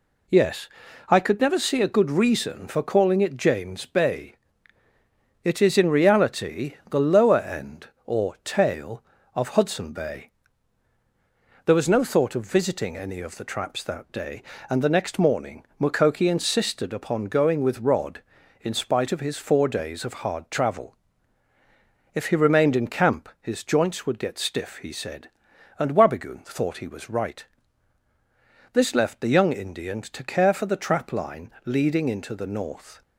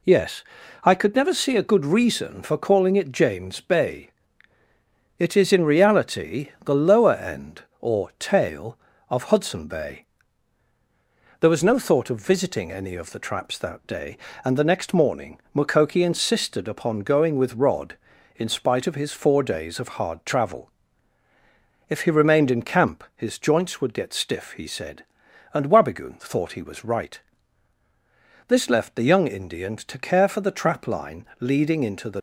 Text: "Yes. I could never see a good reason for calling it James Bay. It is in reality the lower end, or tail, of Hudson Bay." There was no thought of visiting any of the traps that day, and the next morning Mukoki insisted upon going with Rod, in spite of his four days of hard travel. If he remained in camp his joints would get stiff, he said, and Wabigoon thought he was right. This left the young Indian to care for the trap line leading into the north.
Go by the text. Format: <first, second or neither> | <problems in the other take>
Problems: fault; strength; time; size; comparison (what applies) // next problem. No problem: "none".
first | pauses between "reality" and "the"; slight; at 6.4 s; 0.16 s long; slight in the first // pauses between "morning" and "Mukoki"; slight; at 15.3 s; 0.16 s long; slight in the first // pauses between "line" and "leading"; slight; at 31.2 s; 0.16 s long; slight in the first // stops before "north"; at 32.1 s